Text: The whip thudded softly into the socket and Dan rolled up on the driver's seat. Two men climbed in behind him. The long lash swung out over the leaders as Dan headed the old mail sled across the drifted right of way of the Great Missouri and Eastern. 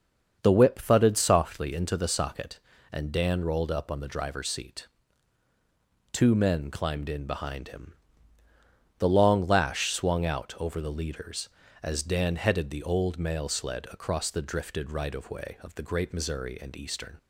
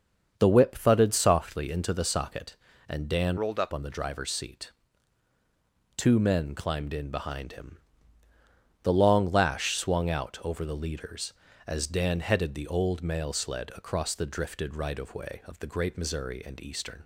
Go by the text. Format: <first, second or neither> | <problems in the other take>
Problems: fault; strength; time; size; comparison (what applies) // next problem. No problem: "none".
first | starts louder than the rest; until 1.3 s; 7 dB; also in the first // changes voice from "rolled" to "up"; from 3.3 to 3.7 s; 0.4 s long